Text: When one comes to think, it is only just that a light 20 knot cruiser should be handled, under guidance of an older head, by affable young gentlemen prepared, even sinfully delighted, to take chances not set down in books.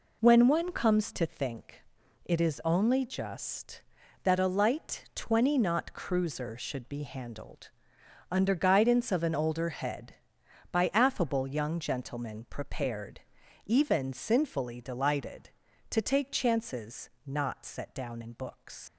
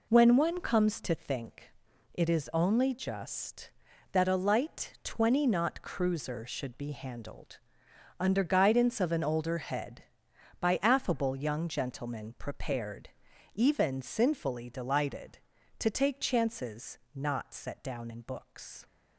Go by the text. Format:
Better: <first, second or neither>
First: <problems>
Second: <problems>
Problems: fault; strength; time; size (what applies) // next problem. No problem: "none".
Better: second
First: pauses between "chances" and "not"; slight; at 17.0 s; 0.18 s long // leaves "books" unfinished; at 18.8 s; 95 ms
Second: pauses between "chances" and "not"; slight; at 16.9 s; 0.18 s long